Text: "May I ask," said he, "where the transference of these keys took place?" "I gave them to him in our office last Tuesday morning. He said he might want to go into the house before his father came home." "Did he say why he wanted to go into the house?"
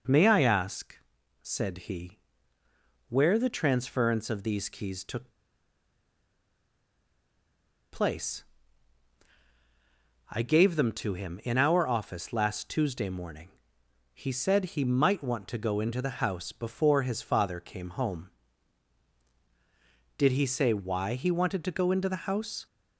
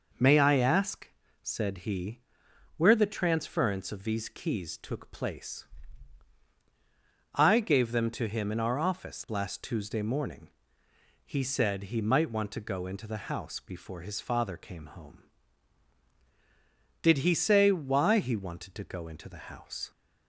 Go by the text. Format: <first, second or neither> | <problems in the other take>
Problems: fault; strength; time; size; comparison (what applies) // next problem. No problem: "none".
second | pauses between "took" and "place"; strong; at 5.3 s; 2.6 s long